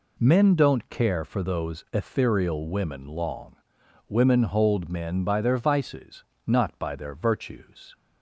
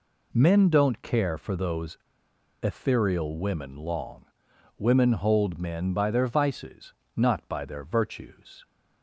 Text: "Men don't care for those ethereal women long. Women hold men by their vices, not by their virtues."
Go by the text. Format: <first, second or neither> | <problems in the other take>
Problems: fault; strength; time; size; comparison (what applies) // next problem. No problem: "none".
first | pauses between "those" and "ethereal"; noticeable; at 1.9 s; 0.66 s long